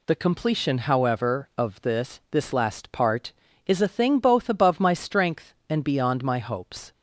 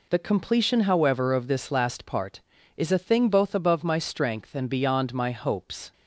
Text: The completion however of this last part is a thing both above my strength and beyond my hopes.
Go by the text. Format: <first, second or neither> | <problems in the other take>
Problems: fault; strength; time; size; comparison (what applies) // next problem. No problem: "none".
second | says "this" twice; at 2.3 s